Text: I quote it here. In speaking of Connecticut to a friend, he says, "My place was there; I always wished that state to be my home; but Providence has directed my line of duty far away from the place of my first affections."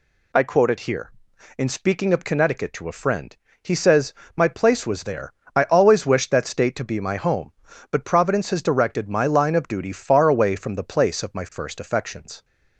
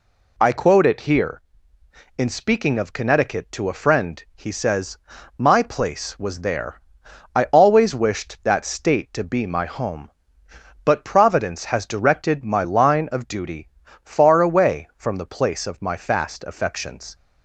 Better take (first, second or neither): first